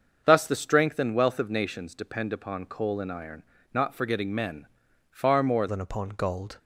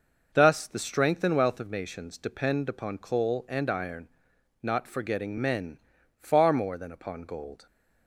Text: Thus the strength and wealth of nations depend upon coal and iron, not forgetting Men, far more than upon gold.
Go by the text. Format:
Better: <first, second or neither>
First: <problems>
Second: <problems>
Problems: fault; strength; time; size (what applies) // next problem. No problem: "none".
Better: second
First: starts louder than the rest; until 1.2 s; 6.5 dB // changes voice at "than"; from 5.6 s on; 0.9 s long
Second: none